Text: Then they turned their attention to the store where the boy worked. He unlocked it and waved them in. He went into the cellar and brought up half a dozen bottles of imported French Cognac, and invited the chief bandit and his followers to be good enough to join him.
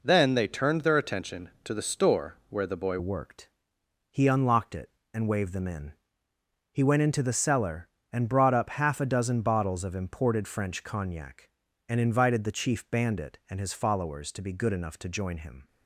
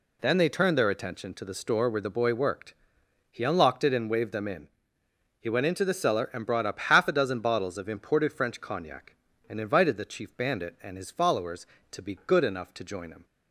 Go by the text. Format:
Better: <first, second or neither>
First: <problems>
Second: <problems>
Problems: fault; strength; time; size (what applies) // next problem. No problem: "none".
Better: second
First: changes voice at "worked"; from 2.9 s on; 12.7 s long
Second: none